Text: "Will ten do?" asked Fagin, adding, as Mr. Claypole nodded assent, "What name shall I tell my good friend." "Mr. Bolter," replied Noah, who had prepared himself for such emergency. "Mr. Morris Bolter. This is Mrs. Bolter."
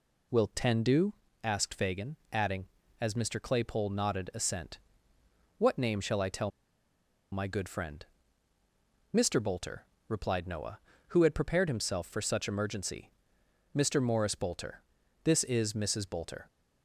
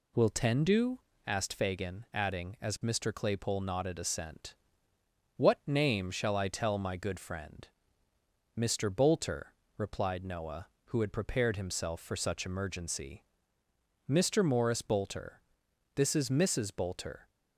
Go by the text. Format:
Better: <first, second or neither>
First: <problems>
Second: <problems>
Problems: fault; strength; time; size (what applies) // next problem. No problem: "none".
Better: second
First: pauses between "tell" and "my"; noticeable; at 6.5 s; 0.82 s long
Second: none